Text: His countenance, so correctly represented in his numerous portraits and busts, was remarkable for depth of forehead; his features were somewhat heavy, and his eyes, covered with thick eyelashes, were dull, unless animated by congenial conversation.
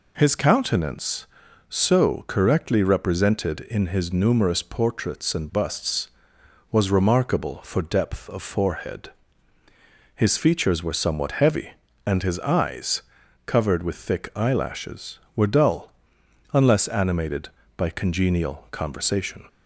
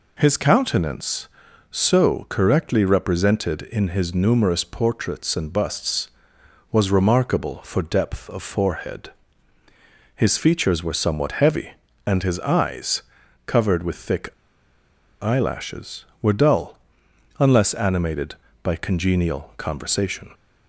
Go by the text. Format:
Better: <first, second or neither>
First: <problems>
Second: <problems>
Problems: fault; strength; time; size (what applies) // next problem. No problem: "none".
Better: first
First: none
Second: pauses between "thick" and "eyelashes"; noticeable; at 14.2 s; 0.91 s long